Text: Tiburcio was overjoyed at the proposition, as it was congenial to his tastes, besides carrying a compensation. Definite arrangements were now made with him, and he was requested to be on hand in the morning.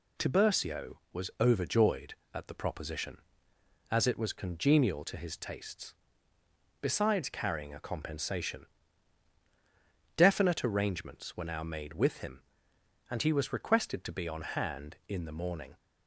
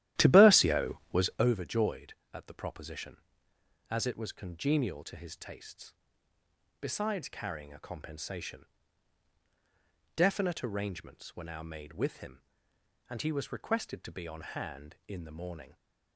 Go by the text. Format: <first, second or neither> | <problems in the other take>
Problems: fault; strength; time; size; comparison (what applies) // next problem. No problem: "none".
first | starts louder than the rest; strong; until 1.5 s; 13 dB